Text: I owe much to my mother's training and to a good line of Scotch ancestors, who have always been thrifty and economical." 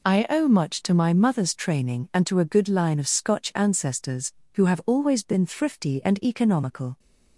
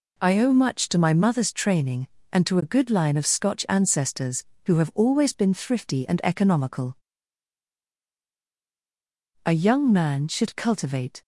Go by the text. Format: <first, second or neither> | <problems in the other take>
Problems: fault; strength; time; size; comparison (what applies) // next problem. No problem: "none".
first | goes on to say "A young man should cultivate"; strong; from 9.4 s on; 1.7 s long